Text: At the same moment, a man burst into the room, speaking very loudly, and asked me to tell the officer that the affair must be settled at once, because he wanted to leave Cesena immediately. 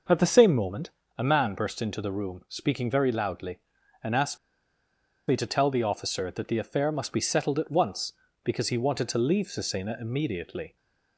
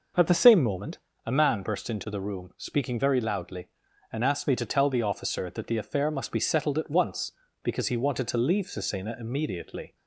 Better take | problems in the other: second | pauses between "asked" and "me"; noticeable; at 4.3 s; 0.89 s long

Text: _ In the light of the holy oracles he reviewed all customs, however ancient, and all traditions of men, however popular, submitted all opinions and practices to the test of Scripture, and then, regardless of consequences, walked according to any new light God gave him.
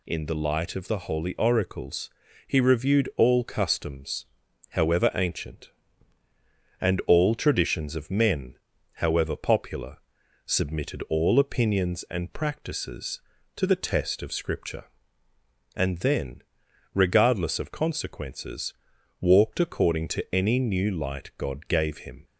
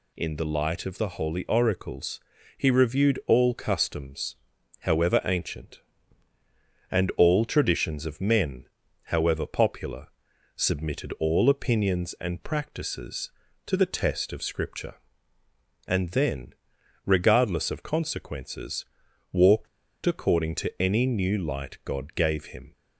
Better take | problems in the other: first | pauses between "oracles" and "he"; at 2.1 s; 0.38 s long; also in the first // pauses between "walked" and "according"; at 19.6 s; 0.38 s long

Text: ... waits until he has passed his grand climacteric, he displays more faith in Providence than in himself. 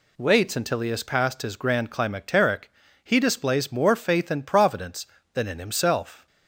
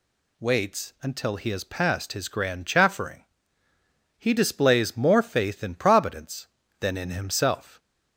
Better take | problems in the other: first | says "chaffering" for "climacteric"; at 2.6 s

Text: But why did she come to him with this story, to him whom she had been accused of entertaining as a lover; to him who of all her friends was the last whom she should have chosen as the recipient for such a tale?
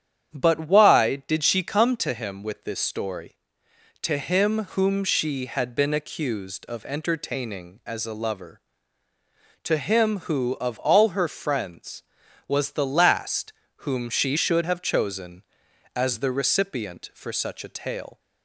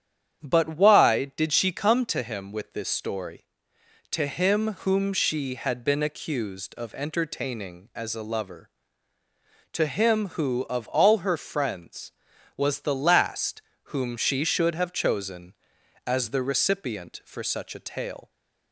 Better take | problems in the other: neither | starts louder than the rest; strong; the same in both // pauses between "last" and "whom"; slight; the same in both

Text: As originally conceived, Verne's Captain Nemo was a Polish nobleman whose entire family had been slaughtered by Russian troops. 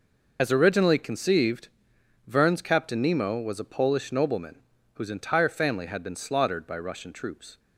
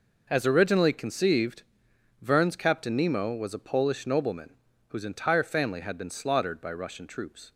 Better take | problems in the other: second | loses the start of "As"; at 0.3 s; 50 ms // pauses between "nobleman" and "whose"; slight; at 4.6 s; 0.34 s long; slight in the second

